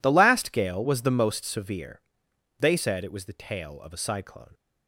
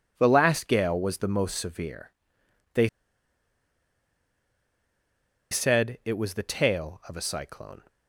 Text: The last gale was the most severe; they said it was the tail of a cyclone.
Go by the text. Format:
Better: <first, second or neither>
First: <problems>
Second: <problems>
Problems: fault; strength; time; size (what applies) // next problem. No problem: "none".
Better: first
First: none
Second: pauses between "they" and "said"; strong; at 2.8 s; 2.6 s long